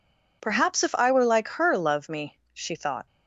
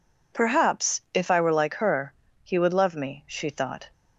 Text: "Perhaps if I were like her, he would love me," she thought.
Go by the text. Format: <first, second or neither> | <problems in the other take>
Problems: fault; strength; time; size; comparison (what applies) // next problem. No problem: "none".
second | skips "he would"; at 1.7 s